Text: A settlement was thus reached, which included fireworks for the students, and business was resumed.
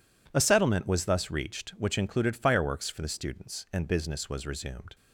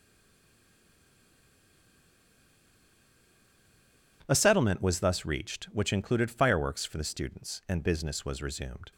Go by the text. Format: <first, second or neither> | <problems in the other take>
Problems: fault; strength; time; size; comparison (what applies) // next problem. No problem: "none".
first | stays silent before the first word; strong; until 4.2 s; 4.2 s long